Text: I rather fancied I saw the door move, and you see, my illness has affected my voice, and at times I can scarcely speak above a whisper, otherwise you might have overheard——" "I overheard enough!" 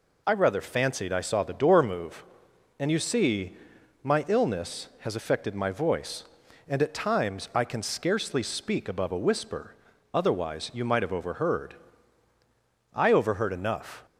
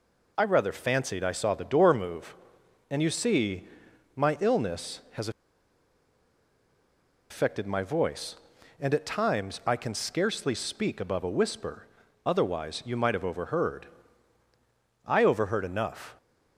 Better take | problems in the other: first | pauses between "has" and "affected"; strong; at 5.2 s; 2.0 s long

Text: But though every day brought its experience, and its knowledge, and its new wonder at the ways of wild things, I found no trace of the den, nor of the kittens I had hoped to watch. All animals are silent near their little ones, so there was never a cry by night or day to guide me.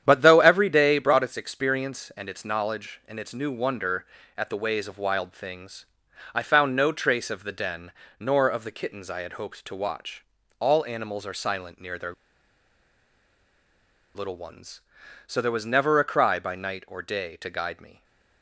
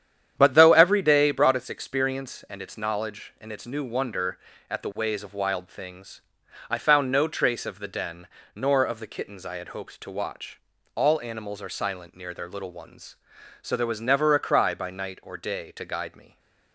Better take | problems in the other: second | starts louder than the rest; strong; until 1.0 s; 9.5 dB; strong in the second // pauses between "their" and "little"; strong; at 12.1 s; 2.0 s long

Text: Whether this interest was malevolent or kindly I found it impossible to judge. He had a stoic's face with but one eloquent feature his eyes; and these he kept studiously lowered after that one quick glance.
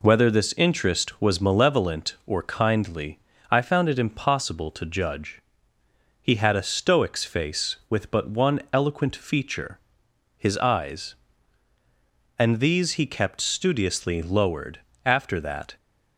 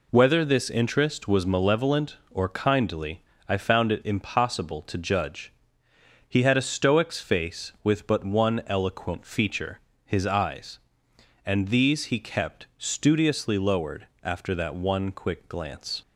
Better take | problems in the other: second | pauses between "kindly" and "I"; slight; at 3.1 s; 0.32 s long; slight in the second // pauses between "feature" and "his"; noticeable; at 9.7 s; 0.60 s long; slight in the second // pauses between "lowered" and "after"; slight; at 14.7 s; 0.26 s long; slight in the second // stops before "one quick glance"; at 15.7 s

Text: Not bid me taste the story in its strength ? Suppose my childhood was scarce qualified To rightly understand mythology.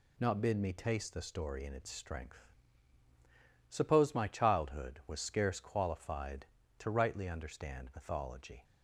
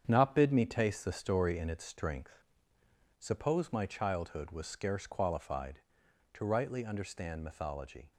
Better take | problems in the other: first | gets quieter; strong; throughout; 7.5 dB

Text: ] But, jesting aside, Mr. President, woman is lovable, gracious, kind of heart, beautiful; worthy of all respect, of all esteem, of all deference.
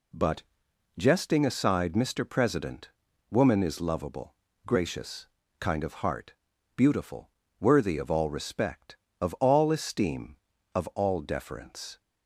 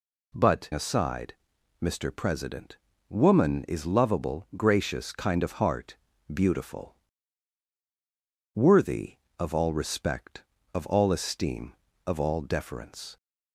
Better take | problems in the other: first | skips "jesting"; at 0.7 s

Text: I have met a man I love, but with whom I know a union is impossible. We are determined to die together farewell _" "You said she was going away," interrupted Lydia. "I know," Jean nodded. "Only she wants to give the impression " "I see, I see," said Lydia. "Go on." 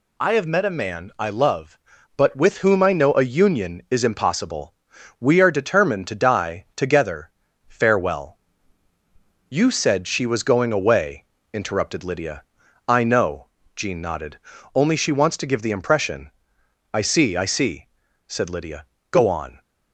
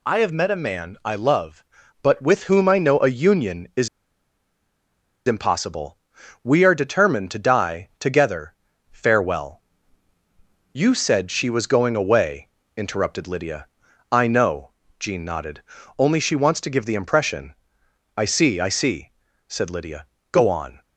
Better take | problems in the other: first | pauses between "is" and "impossible"; strong; at 3.8 s; 1.3 s long // pauses between "together" and "farewell"; at 8.5 s; 0.40 s long; also in the first

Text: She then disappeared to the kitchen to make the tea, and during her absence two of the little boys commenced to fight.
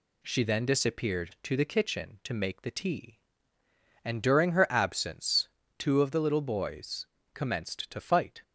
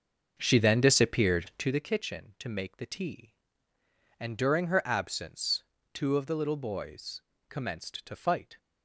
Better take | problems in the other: first | starts louder than the rest; until 1.8 s; 6 dB // pauses between "absence" and "two"; slight; at 5.6 s; 0.30 s long; slight in the first // pauses between "boys" and "commenced"; slight; at 7.2 s; 0.28 s long; slight in the first

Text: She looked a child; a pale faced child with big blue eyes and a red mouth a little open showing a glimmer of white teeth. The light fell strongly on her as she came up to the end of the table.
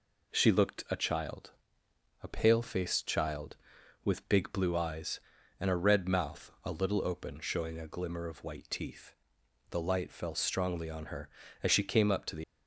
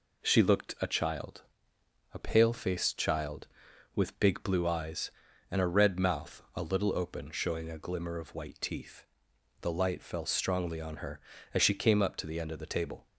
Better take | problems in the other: second | stops before "end of the table"; at 12.4 s

